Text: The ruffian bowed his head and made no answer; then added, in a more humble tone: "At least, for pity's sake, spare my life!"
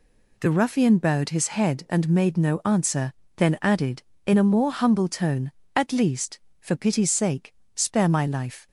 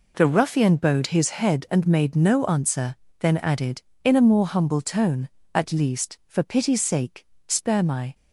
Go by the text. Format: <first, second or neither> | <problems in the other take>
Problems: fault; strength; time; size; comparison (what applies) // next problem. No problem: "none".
first | stops before "life"; at 8.1 s